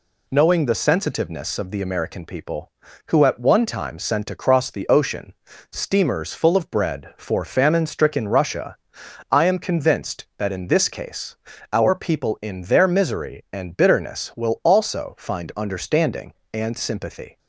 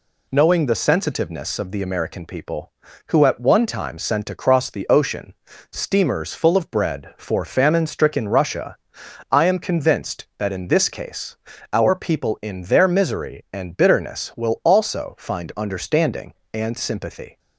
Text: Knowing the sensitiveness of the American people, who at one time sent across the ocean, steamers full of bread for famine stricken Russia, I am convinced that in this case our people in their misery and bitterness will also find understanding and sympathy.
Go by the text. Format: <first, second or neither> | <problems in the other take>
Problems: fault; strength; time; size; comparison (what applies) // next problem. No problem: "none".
neither | pauses between "case" and "our"; slight; the same in both